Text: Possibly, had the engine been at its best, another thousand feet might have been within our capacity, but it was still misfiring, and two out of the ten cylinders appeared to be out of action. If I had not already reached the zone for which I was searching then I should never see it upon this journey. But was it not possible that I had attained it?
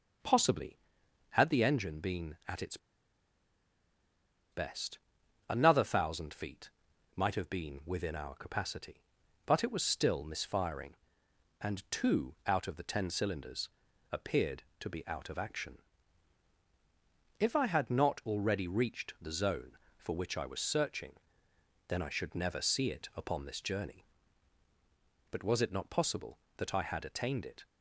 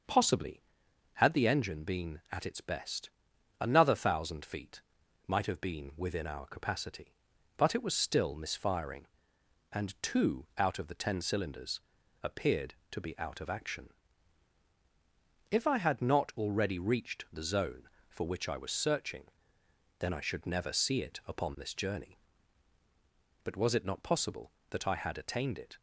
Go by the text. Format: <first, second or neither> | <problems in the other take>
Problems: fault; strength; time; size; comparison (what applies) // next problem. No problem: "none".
second | starts louder than the rest; until 1.7 s; 6.5 dB; also in the second // pauses between "its" and "best"; strong; at 2.7 s; 1.7 s long // pauses between "feet" and "might"; at 6.7 s; 0.44 s long; also in the second // pauses between "cylinders" and "appeared"; at 13.6 s; 0.42 s long; also in the second // pauses between "searching" and "then"; noticeable; at 21.1 s; 0.76 s long; noticeable in the second